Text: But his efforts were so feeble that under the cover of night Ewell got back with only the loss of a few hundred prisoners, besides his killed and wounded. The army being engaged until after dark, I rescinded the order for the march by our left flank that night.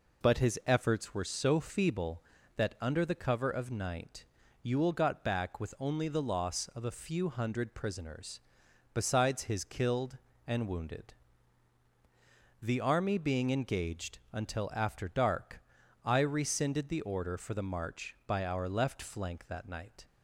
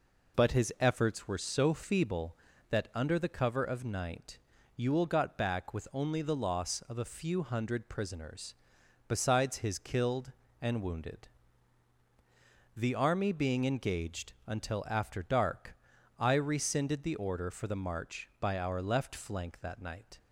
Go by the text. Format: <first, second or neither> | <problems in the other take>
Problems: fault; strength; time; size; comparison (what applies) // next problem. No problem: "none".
neither | pauses between "night" and "Ewell"; the same in both